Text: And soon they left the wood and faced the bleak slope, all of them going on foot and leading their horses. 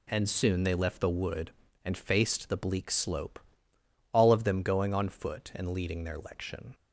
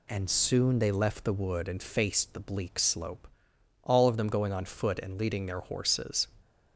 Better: second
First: says "lection" for "horses"; at 6.1 s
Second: none

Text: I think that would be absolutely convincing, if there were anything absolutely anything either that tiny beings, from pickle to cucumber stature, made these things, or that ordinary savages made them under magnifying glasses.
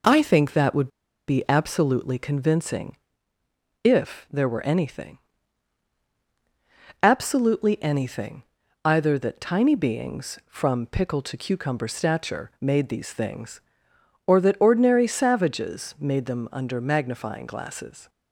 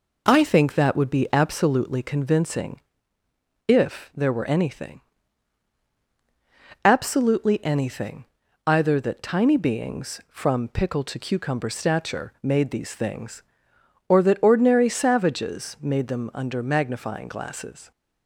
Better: second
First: pauses between "would" and "be"; at 0.8 s; 0.40 s long // pauses between "anything" and "absolutely"; strong; at 5.1 s; 1.8 s long // pauses between "anything" and "either"; at 8.4 s; 0.42 s long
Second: pauses between "anything" and "absolutely"; strong; at 5.0 s; 1.8 s long // pauses between "anything" and "either"; at 8.2 s; 0.42 s long

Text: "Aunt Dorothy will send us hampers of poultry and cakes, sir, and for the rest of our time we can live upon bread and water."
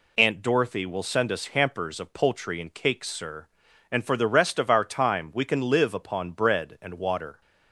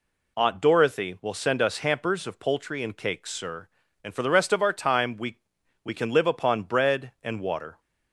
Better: first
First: none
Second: says "we" twice; at 5.8 s

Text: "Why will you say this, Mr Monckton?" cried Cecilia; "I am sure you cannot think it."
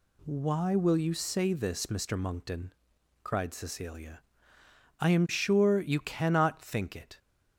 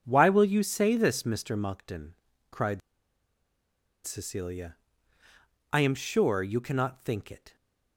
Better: first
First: none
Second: pauses between "cried" and "Cecilia"; strong; at 2.8 s; 1.2 s long

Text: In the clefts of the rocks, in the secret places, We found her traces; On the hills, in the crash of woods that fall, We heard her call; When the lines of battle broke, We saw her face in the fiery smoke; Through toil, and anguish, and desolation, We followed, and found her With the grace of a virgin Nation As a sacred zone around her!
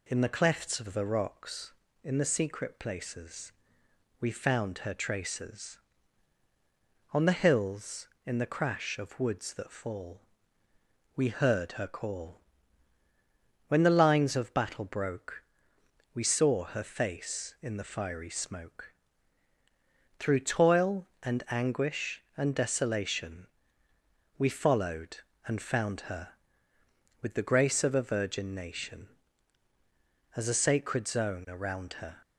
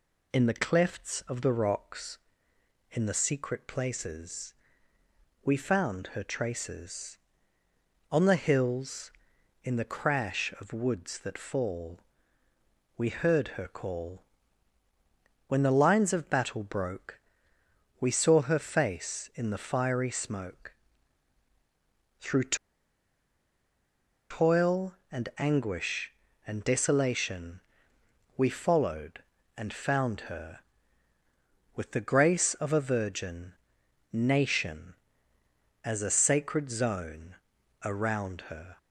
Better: first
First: none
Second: pauses between "Through" and "toil"; strong; at 22.5 s; 1.7 s long // pauses between "virgin" and "Nation"; noticeable; at 33.5 s; 0.58 s long // pauses between "zone" and "around"; noticeable; at 37.3 s; 0.48 s long

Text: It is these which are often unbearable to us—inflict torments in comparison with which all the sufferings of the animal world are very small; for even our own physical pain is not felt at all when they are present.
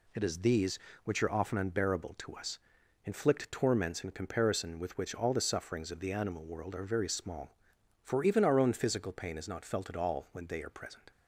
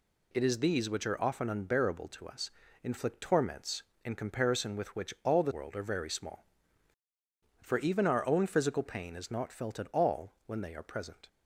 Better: first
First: none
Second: skips "sufferings of the animal"; at 5.5 s

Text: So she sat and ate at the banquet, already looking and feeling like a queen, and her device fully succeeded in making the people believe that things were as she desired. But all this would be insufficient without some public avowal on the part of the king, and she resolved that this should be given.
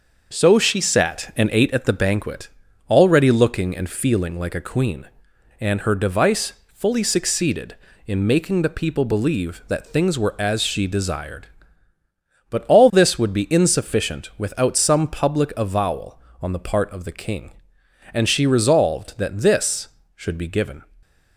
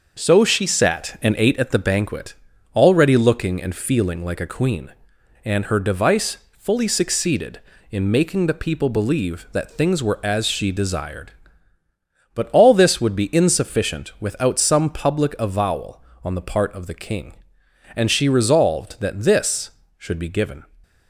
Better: neither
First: starts louder than the rest; until 1.3 s; 6 dB // pauses between "device" and "fully"; slight; at 6.5 s; 0.18 s long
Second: starts louder than the rest; until 1.2 s; 6 dB // pauses between "device" and "fully"; slight; at 6.3 s; 0.18 s long

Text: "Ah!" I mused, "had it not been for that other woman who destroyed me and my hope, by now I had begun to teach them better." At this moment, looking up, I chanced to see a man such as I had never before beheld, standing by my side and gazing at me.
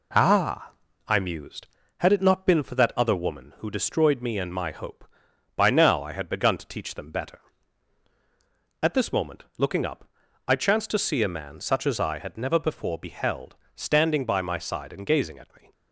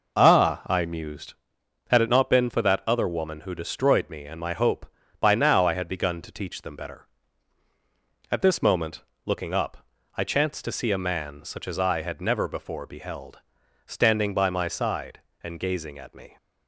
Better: neither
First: none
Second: none

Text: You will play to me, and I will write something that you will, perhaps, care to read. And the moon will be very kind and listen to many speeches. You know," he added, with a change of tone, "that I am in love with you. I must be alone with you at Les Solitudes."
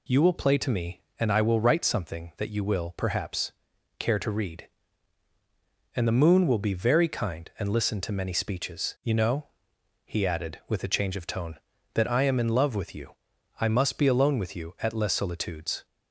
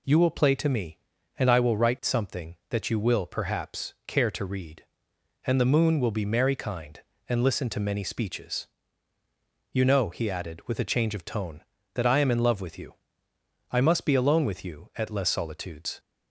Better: first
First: none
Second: says "merry" for "very"; at 6.2 s

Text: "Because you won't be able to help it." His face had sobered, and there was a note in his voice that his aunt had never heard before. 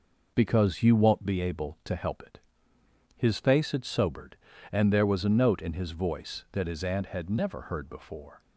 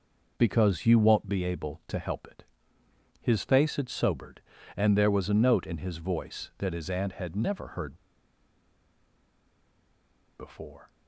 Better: first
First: none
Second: pauses between "heard" and "before"; strong; at 7.9 s; 2.4 s long

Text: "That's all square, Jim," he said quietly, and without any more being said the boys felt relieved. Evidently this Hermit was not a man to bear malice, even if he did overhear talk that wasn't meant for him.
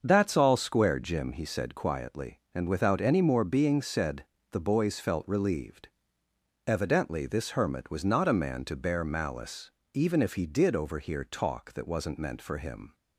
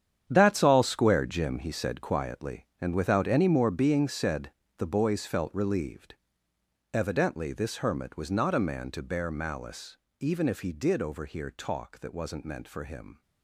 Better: first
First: starts louder than the rest; until 1.0 s; 6.5 dB // pauses between "said" and "the"; slight; at 4.2 s; 0.28 s long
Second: gets quieter; strong; throughout; 13 dB // starts louder than the rest; strong; until 1.2 s; 9 dB // pauses between "said" and "the"; slight; at 4.5 s; 0.28 s long

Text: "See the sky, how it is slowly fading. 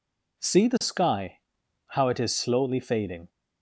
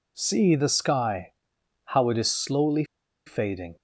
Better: first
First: none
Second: pauses between "slowly" and "fading"; at 2.8 s; 0.41 s long

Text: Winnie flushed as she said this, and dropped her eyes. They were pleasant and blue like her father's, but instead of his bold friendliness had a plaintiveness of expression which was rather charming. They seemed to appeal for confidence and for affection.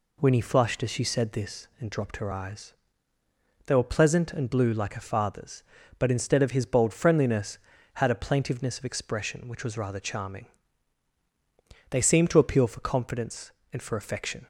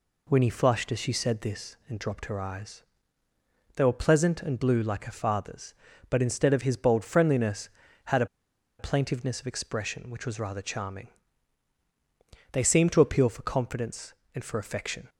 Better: first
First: none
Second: pauses between "a" and "plaintiveness"; noticeable; at 8.2 s; 0.53 s long

